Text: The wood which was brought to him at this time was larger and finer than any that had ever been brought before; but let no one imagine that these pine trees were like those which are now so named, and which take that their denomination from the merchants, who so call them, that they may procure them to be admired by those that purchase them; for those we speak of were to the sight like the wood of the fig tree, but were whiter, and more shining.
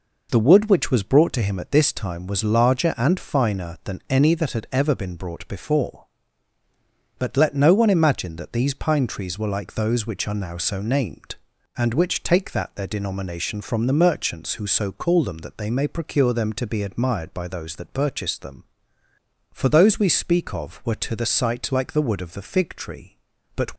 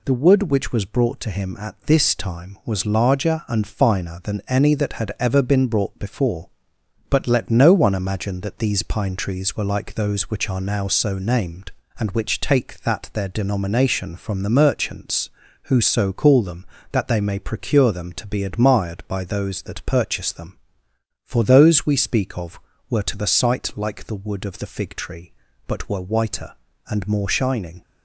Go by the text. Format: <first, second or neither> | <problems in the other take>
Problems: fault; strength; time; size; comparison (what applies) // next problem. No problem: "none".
second | stops before "were whiter and more shining"; at 23.7 s